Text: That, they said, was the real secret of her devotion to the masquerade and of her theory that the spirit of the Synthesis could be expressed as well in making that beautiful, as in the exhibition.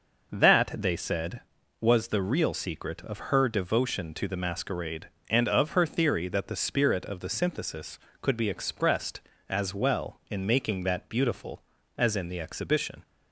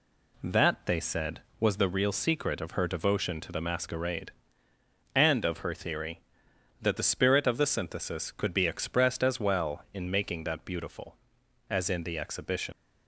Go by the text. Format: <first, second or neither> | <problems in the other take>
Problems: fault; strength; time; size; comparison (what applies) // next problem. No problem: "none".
first | leaves "exhibition" unfinished; at 12.7 s; 110 ms